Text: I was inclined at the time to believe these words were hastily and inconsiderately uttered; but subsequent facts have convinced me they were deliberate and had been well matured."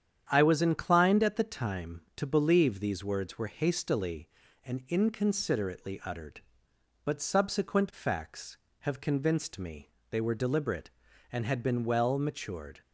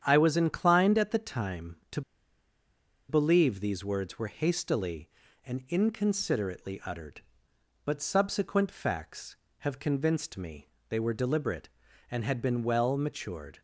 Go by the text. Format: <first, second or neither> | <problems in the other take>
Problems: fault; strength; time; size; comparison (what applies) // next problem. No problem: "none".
first | starts louder than the rest; strong; until 1.0 s; 9 dB; strong in the first // pauses between "to" and "believe"; at 2.0 s; 1.0 s long // pauses between "me" and "they"; slight; at 10.6 s; 0.22 s long; slight in the first